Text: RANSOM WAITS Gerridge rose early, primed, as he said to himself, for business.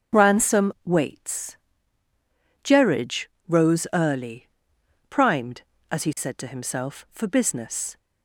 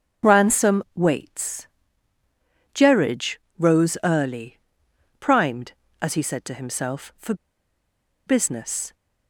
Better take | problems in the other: first | starts louder than the rest; strong; until 1.3 s; 7.5 dB; strong in the first // pauses between "WAITS" and "Gerridge"; at 1.6 s; 1.0 s long; also in the first // pauses between "Gerridge" and "rose"; slight; at 3.3 s; 0.22 s long; slight in the first // pauses between "for" and "business"; noticeable; at 7.3 s; 0.92 s long

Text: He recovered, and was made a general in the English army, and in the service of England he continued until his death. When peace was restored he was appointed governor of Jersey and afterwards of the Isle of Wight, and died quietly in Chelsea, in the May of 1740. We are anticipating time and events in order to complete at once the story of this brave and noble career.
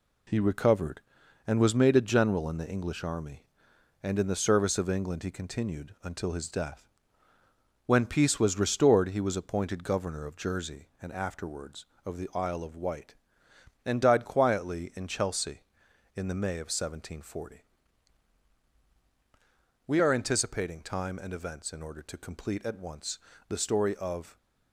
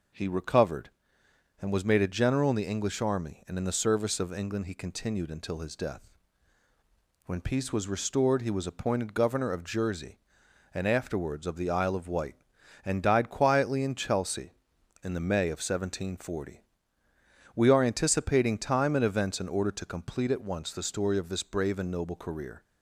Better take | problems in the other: second | pauses between "once" and "the"; slight; at 23.1 s; 0.28 s long // stops before "this brave and noble career"; at 24.3 s

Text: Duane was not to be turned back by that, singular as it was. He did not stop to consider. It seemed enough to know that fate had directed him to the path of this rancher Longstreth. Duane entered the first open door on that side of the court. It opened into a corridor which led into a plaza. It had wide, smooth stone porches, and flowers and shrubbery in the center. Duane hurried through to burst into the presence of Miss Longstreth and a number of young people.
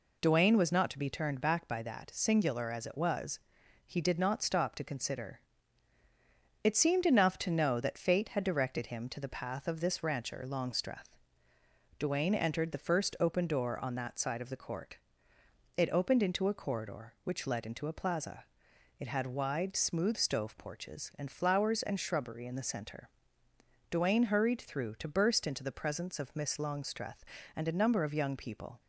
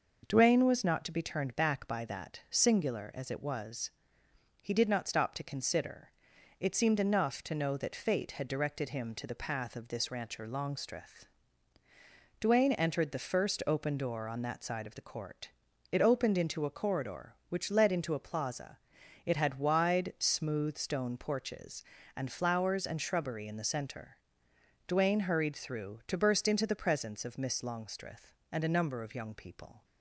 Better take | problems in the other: second | says "stove" for "stone"; at 20.1 s

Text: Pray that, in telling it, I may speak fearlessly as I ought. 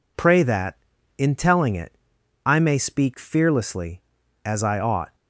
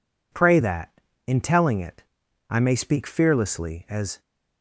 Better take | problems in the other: first | stops before "I ought"; at 4.2 s

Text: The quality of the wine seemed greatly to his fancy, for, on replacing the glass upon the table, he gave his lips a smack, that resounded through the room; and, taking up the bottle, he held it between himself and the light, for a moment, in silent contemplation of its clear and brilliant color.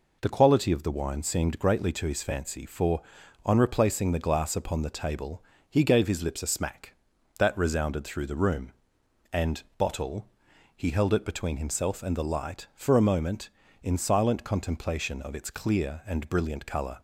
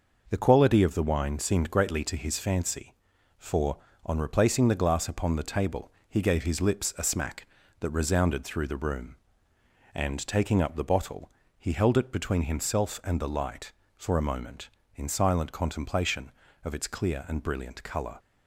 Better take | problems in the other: second | skips "taking up the"; at 9.6 s

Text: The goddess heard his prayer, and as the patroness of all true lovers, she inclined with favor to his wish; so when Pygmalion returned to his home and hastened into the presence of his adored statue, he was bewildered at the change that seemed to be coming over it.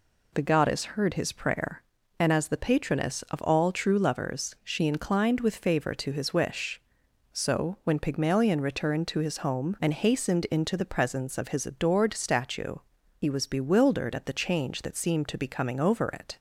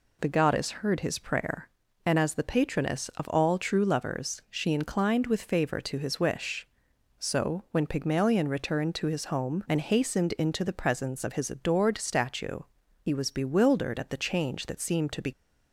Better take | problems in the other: first | stops before "coming over it"; at 15.3 s

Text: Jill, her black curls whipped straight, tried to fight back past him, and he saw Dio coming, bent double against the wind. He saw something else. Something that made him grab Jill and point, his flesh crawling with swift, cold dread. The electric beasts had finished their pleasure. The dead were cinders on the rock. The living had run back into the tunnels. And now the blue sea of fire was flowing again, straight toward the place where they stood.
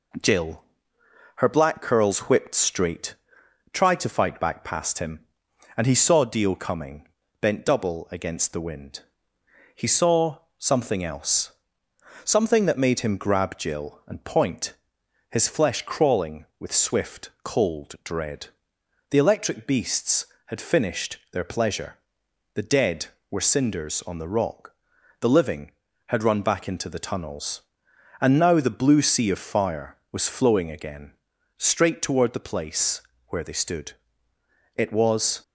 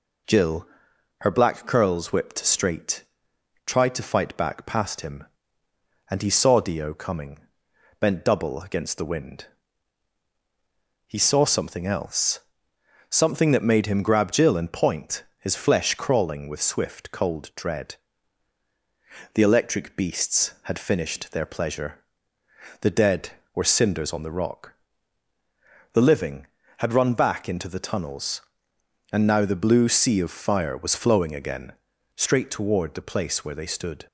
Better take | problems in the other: second | pauses between "saw" and "something"; slight; at 10.3 s; 0.20 s long // pauses between "finished" and "their"; slight; at 21.1 s; 0.16 s long // pauses between "place" and "where"; slight; at 33.0 s; 0.28 s long // goes on to say "It was"; noticeable; from 34.7 s on; 0.66 s long

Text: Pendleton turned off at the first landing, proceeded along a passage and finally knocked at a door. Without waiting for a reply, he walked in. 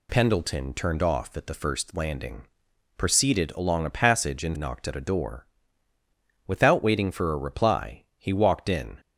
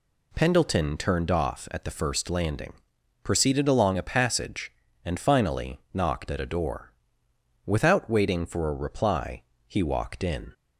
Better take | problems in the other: second | skips "finally"; at 4.5 s

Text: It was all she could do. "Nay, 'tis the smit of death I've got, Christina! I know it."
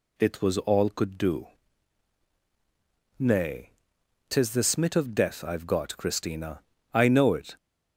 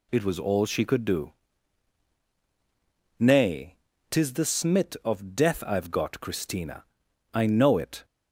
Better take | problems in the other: second | skips "she"; at 0.8 s

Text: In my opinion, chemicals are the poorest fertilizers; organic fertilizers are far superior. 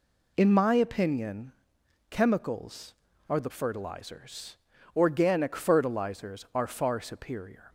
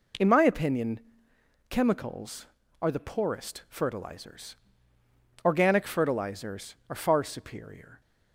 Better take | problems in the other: second | skips "poorest"; at 3.5 s

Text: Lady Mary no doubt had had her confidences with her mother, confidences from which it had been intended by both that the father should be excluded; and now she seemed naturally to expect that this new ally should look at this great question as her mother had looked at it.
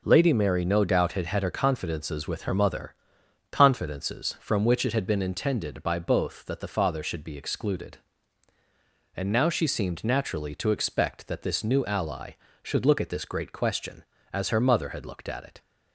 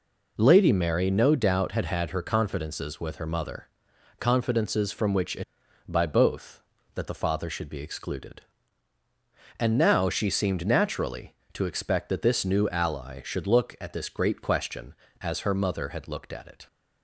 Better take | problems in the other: first | skips "had been intended"; at 5.6 s

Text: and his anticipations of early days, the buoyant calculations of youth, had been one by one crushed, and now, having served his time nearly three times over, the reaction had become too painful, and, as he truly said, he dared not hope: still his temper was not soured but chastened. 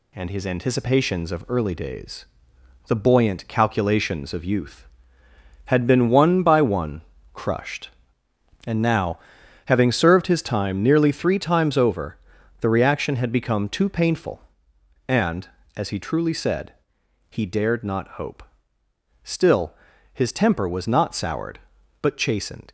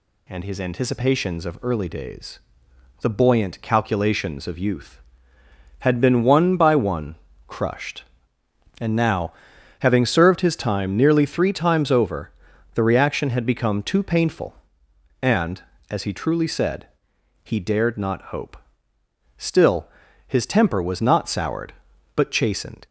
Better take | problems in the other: second | gets quieter; slight; throughout; 2.5 dB // pauses between "one" and "crushed"; slight; at 7.0 s; 0.30 s long; slight in the second // pauses between "still" and "his"; at 19.7 s; 0.40 s long; also in the second

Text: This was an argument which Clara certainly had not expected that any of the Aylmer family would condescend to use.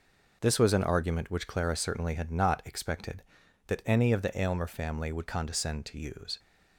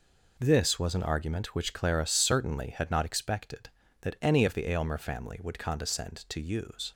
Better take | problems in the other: neither | none

